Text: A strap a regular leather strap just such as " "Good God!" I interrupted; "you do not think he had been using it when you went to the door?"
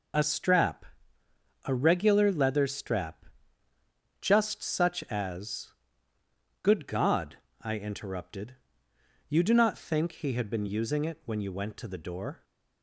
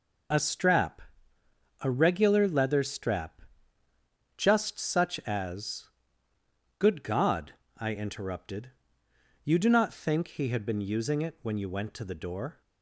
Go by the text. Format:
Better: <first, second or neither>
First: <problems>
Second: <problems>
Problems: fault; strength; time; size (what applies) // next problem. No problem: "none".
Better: neither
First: pauses between "strap" and "a"; noticeable; at 0.8 s; 0.80 s long // pauses between "strap" and "just"; noticeable; at 3.2 s; 0.96 s long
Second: pauses between "strap" and "a"; noticeable; at 1.0 s; 0.80 s long // pauses between "strap" and "just"; noticeable; at 3.4 s; 0.96 s long